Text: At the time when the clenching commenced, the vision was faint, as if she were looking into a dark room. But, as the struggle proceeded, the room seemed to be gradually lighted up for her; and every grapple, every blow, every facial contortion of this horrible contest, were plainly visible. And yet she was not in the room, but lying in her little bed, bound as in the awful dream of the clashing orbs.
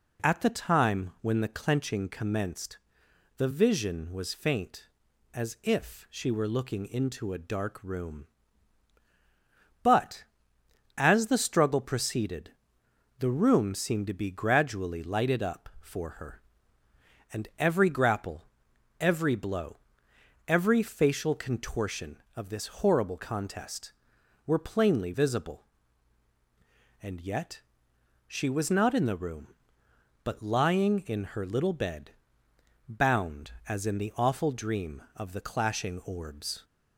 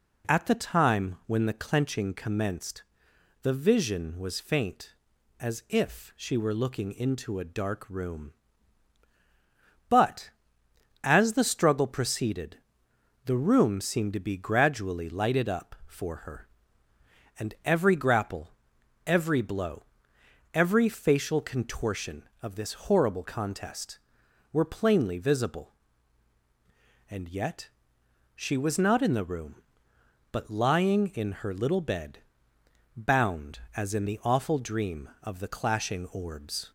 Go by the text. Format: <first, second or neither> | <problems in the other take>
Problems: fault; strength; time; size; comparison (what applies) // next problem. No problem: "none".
neither | pauses between "yet" and "she"; noticeable; the same in both